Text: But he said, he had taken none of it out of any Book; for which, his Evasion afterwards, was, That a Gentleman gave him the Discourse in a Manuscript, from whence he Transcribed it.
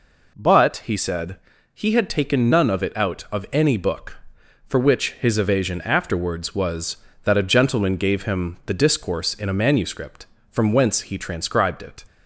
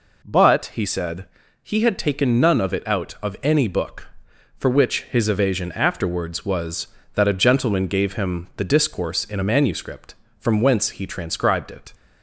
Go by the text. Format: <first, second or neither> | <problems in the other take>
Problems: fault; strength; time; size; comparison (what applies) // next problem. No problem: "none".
neither | none